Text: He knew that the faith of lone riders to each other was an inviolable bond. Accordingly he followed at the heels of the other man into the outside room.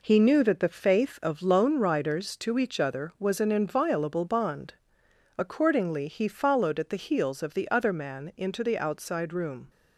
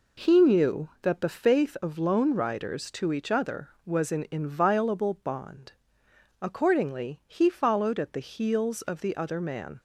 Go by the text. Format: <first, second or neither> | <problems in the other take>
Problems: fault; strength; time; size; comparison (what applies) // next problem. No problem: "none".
first | stops before "into the outside room"; at 9.7 s